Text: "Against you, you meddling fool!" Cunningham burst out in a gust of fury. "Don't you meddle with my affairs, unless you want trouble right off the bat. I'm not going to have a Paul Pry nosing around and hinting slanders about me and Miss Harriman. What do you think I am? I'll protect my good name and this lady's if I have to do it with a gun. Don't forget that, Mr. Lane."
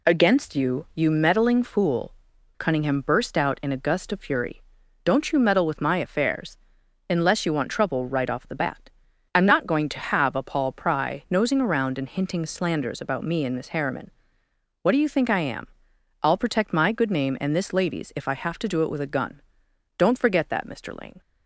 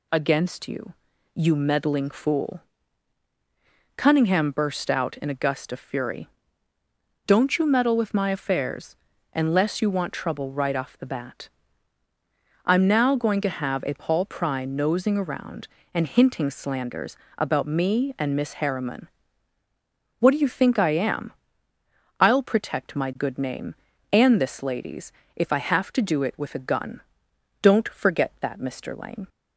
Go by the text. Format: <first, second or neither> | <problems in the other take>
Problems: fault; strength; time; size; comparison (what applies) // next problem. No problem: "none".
first | says "now" for "not"; at 12.8 s // pauses between "slanders" and "about"; slight; at 17.1 s; 0.20 s long // pauses between "lady's" and "if"; slight; at 25.1 s; 0.24 s long